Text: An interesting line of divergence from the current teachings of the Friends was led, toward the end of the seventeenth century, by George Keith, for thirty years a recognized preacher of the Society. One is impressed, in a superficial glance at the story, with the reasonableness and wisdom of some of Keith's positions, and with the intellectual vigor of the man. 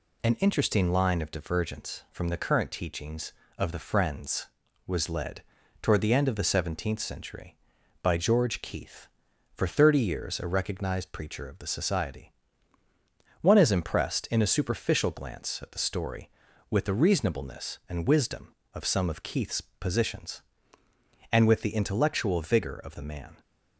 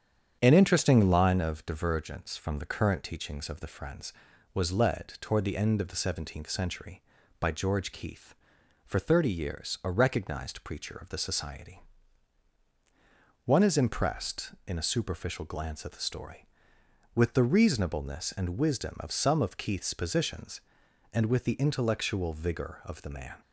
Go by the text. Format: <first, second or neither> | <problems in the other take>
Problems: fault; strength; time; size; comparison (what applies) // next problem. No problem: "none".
first | starts louder than the rest; strong; until 1.6 s; 8.5 dB